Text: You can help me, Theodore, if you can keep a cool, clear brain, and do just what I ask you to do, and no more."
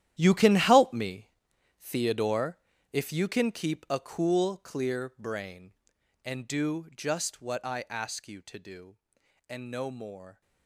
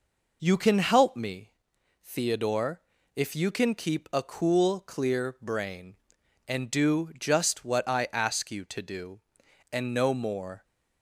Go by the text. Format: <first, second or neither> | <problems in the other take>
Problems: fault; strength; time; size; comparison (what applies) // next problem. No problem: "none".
second | gets quieter; strong; throughout; 14.5 dB